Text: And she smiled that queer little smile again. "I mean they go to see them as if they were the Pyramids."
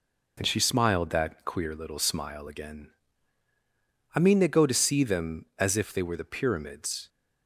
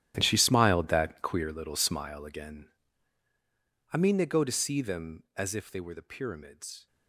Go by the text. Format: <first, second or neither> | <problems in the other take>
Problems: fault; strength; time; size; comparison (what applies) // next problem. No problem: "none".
first | gets quieter; strong; throughout; 15.5 dB